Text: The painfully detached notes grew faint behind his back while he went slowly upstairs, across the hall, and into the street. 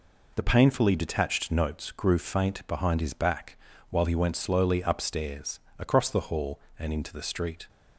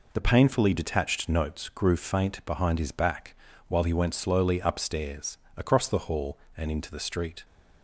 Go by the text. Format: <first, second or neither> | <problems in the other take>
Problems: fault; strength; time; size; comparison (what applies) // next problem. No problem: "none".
neither | pauses between "back" and "while"; slight; the same in both